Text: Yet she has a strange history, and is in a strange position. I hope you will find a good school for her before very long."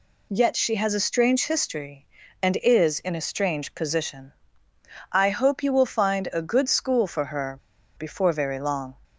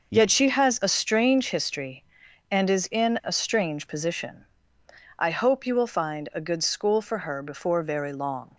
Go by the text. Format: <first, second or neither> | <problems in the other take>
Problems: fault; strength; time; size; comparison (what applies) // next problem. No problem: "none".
second | pauses between "her" and "before"; at 7.5 s; 0.38 s long